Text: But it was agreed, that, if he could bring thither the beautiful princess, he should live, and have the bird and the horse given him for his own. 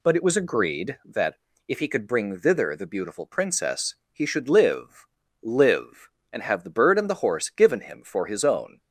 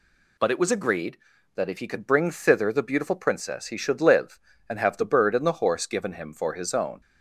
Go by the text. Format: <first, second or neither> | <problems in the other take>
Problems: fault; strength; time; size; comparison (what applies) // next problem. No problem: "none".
second | says "live" twice; at 5.4 s